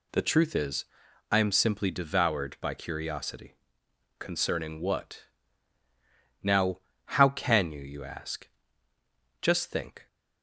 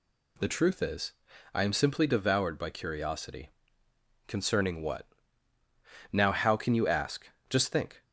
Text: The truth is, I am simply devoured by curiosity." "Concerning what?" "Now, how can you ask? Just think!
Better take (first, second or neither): second